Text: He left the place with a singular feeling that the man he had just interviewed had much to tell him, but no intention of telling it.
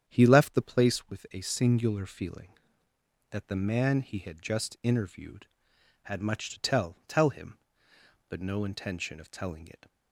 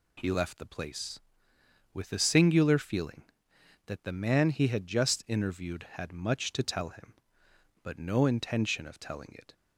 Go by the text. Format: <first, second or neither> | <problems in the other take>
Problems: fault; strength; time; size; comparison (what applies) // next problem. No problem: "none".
second | starts louder than the rest; strong; until 1.0 s; 9 dB // says "tell" twice; at 7.0 s